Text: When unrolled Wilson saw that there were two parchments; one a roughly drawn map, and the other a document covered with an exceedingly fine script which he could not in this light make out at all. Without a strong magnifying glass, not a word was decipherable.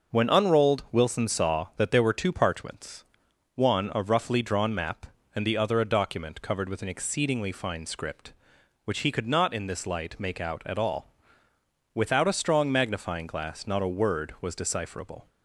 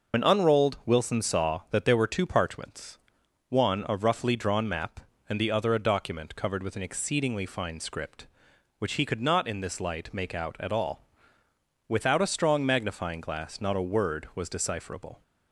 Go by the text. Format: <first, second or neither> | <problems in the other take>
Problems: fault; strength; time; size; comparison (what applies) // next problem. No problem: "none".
first | loses the start of "When"; at 0.1 s; 75 ms